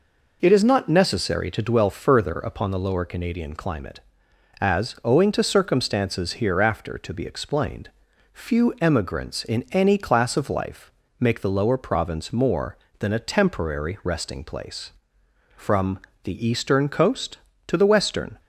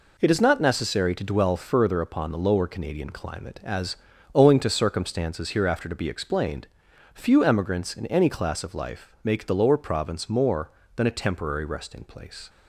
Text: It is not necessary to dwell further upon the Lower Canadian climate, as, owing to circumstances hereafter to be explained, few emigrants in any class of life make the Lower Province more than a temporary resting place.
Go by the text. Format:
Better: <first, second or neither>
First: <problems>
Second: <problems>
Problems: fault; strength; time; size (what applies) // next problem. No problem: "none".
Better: second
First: pauses between "life" and "make"; slight; at 10.9 s; 0.28 s long // goes on to say "From the eastern coast to the western"; strong; from 15.5 s on; 2.8 s long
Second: none